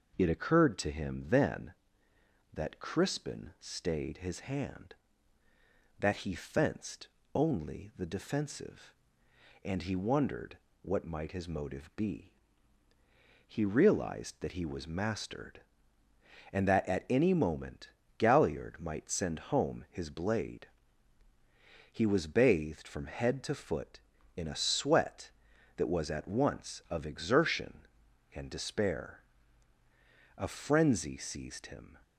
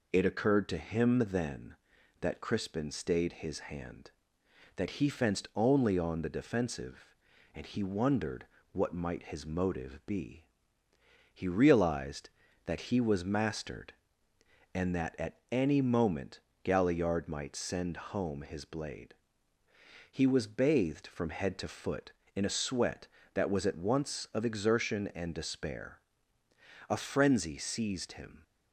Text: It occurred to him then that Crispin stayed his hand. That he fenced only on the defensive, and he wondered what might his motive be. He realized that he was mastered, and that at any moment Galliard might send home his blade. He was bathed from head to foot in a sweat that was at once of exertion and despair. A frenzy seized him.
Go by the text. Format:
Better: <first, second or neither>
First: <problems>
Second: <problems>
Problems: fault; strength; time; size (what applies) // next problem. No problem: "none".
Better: second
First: pauses between "fenced" and "only"; slight; at 7.0 s; 0.26 s long // skips "on"; at 7.9 s // pauses between "wondered" and "what"; slight; at 10.5 s; 0.24 s long // pauses between "moment" and "Galliard"; slight; at 17.8 s; 0.30 s long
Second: pauses between "wondered" and "what"; slight; at 8.4 s; 0.28 s long // pauses between "moment" and "Galliard"; slight; at 16.4 s; 0.22 s long